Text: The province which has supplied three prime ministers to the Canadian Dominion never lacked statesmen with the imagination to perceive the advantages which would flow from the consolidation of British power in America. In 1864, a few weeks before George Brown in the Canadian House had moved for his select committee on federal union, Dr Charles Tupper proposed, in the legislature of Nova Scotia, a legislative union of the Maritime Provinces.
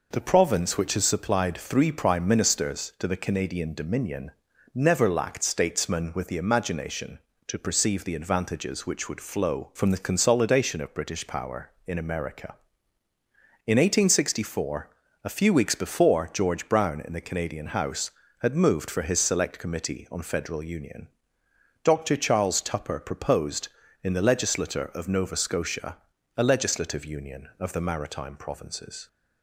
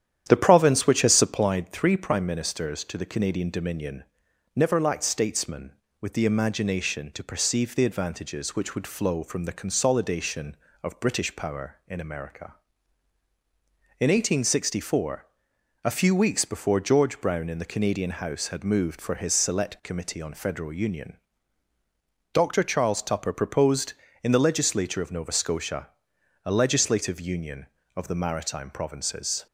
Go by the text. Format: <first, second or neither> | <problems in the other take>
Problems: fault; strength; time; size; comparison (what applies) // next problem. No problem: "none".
first | starts louder than the rest; strong; until 1.6 s; 10 dB // pauses between "Dominion" and "never"; noticeable; at 4.0 s; 0.54 s long; also in the first